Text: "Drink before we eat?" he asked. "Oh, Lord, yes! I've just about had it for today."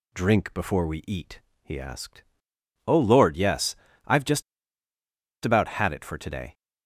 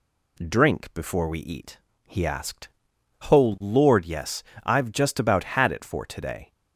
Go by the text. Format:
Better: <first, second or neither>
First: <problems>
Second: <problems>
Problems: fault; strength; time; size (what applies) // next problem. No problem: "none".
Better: second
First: pauses between "just" and "about"; at 4.4 s; 1.0 s long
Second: none